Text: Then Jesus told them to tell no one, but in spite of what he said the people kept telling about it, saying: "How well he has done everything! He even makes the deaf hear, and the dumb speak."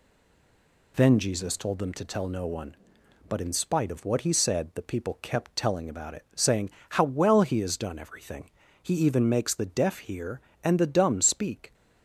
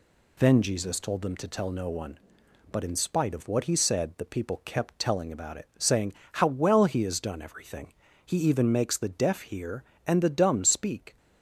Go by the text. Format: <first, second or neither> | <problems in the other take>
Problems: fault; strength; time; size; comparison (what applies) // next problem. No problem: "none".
second | stays silent before the first word; slight; until 0.9 s; 0.9 s long